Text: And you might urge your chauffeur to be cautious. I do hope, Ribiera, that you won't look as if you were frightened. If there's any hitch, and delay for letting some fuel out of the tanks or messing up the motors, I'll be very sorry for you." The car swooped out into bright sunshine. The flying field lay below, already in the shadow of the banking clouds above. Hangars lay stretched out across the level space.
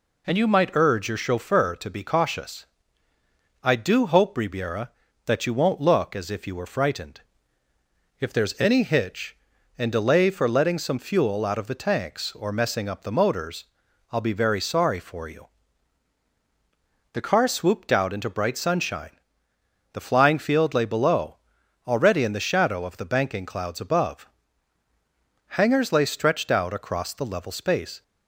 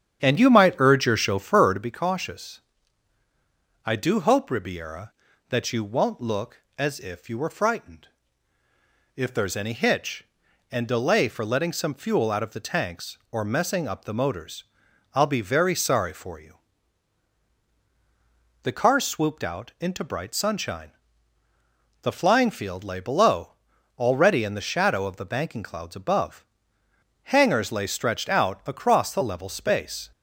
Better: first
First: none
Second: starts louder than the rest; strong; until 1.9 s; 9 dB

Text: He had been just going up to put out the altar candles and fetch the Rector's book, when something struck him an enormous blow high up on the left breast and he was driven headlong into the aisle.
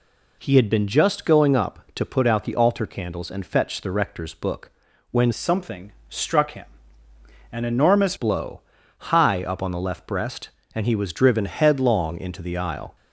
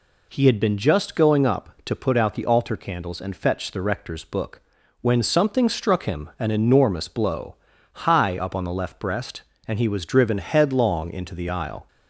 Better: second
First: changes voice from "something" to "enormous"; from 5.3 to 8.1 s; 2.8 s long // pauses between "something" and "struck"; slight; at 5.9 s; 0.18 s long // pauses between "him" and "an"; noticeable; at 6.6 s; 0.86 s long // pauses between "blow" and "high"; noticeable; at 8.6 s; 0.48 s long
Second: pauses between "blow" and "high"; noticeable; at 7.5 s; 0.48 s long

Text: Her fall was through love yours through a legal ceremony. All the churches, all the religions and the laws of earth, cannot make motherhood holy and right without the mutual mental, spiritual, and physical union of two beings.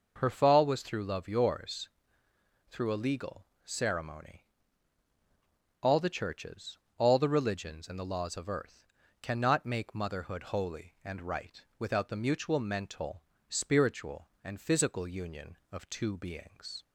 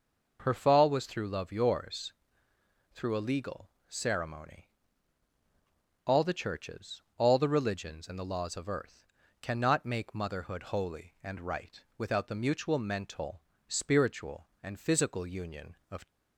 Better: first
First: pauses between "yours" and "through"; noticeable; at 1.8 s; 0.82 s long // pauses between "legal" and "ceremony"; slight; at 3.4 s; 0.20 s long // pauses between "right" and "without"; slight; at 11.6 s; 0.18 s long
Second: pauses between "yours" and "through"; noticeable; at 2.1 s; 0.82 s long // pauses between "legal" and "ceremony"; slight; at 3.6 s; 0.20 s long // pauses between "right" and "without"; slight; at 11.7 s; 0.18 s long // stops before "two beings"; at 16.0 s

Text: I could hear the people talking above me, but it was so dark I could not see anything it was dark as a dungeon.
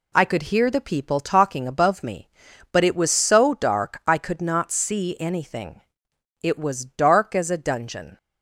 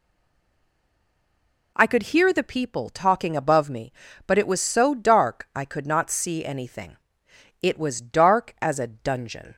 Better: first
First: pauses between "anything" and "it"; noticeable; at 5.8 s; 0.60 s long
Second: stays silent before the first word; noticeable; until 1.7 s; 1.7 s long // pauses between "anything" and "it"; noticeable; at 6.9 s; 0.64 s long

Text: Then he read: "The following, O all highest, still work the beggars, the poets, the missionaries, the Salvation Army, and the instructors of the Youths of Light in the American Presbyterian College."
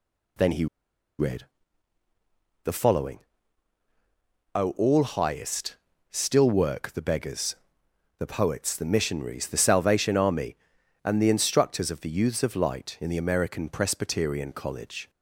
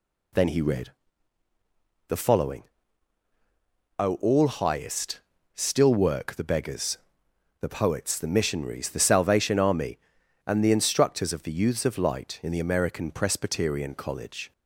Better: second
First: pauses between "he" and "read"; noticeable; at 0.6 s; 0.53 s long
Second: none

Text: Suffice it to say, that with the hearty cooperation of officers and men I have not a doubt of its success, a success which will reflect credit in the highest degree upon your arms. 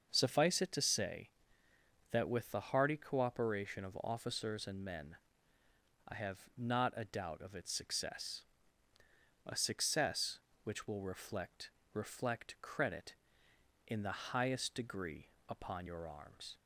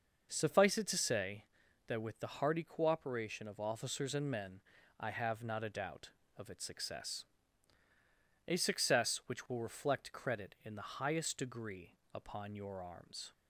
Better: second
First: starts louder than the rest; until 1.1 s; 6 dB // pauses between "men" and "I"; noticeable; at 5.1 s; 0.96 s long // pauses between "have" and "not"; slight; at 6.3 s; 0.18 s long // says "reflect" twice; at 11.9 s // pauses between "degree" and "upon"; slight; at 15.2 s; 0.22 s long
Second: starts louder than the rest; noticeable; until 1.3 s; 6 dB // pauses between "men" and "I"; at 4.5 s; 0.40 s long // pauses between "degree" and "upon"; slight; at 11.9 s; 0.18 s long

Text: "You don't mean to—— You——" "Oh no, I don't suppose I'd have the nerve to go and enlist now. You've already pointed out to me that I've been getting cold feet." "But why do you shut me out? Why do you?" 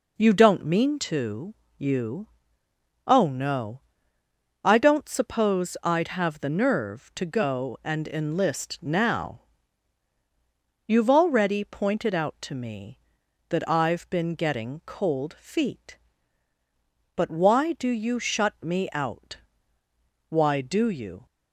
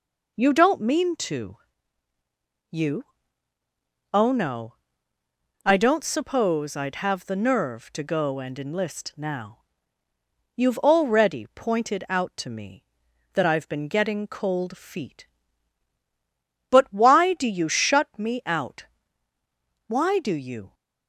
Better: neither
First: none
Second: none

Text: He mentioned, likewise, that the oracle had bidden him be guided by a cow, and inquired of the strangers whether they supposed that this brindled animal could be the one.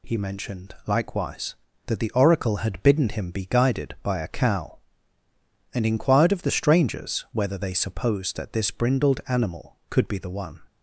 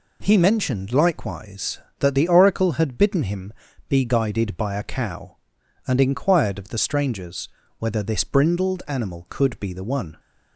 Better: first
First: none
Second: pauses between "him" and "be"; at 3.5 s; 0.38 s long // pauses between "strangers" and "whether"; slight; at 7.4 s; 0.30 s long // skips "they supposed that"; at 8.0 s

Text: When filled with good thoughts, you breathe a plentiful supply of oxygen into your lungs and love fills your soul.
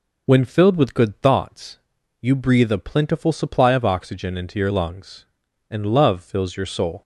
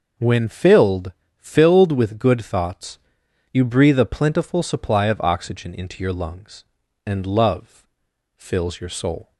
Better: first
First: none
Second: says "filled" twice; at 1.3 s // pauses between "love" and "fills"; noticeable; at 7.8 s; 0.48 s long

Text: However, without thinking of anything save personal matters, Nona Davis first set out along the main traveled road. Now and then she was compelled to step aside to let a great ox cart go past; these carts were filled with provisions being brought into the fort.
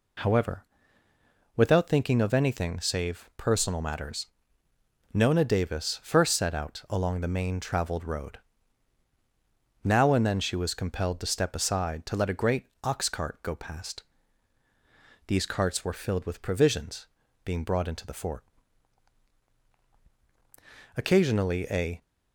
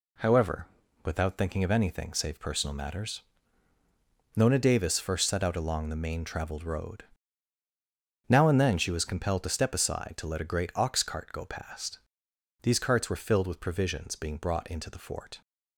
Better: second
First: pauses between "great" and "ox"; slight; at 12.6 s; 0.16 s long // pauses between "provisions" and "being"; at 17.0 s; 0.38 s long // goes on to say "Occasionally a"; noticeable; from 20.9 s on; 1.0 s long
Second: none

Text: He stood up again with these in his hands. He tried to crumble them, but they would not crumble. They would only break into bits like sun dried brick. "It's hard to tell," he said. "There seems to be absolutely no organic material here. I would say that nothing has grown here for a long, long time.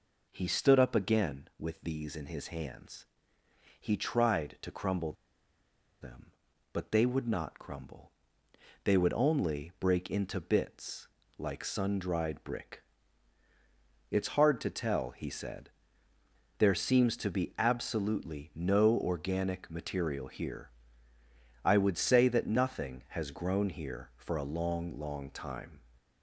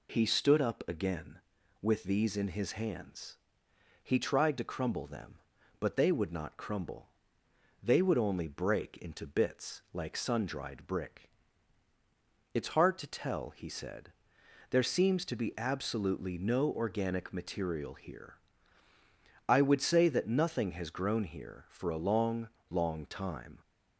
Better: second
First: pauses between "crumble" and "them"; noticeable; at 5.1 s; 0.88 s long // pauses between "bits" and "like"; slight; at 11.0 s; 0.30 s long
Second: none

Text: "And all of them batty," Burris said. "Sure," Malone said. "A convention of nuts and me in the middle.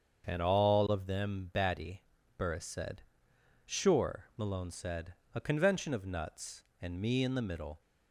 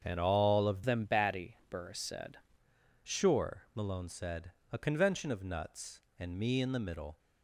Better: first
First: starts louder than the rest; until 1.3 s; 7 dB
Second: starts louder than the rest; until 1.0 s; 7 dB // changes voice from "them" to "said"; from 0.8 to 2.3 s; 1.5 s long

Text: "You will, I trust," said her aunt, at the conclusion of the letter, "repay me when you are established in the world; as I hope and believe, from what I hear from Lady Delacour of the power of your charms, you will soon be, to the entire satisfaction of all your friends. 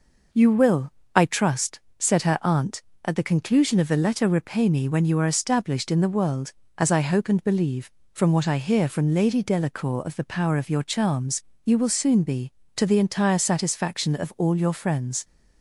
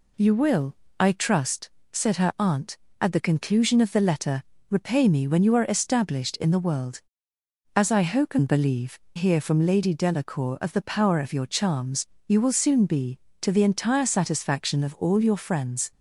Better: first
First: none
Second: skips "from what I"; at 9.0 s

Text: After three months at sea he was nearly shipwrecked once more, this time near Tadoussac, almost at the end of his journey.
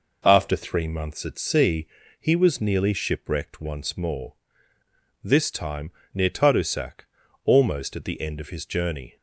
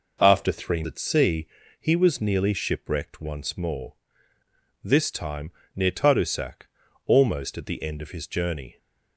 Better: first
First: pauses between "sea" and "he"; slight; at 1.8 s; 0.34 s long // pauses between "time" and "near"; slight; at 5.9 s; 0.22 s long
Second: skips "months"; at 0.8 s // pauses between "sea" and "he"; slight; at 1.4 s; 0.34 s long // pauses between "time" and "near"; slight; at 5.5 s; 0.24 s long

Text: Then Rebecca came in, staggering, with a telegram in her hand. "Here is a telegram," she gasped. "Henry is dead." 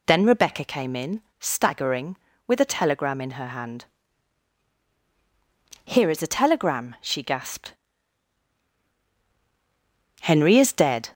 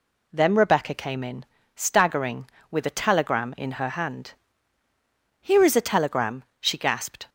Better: first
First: none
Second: stops before "Henry is dead"; at 7.2 s

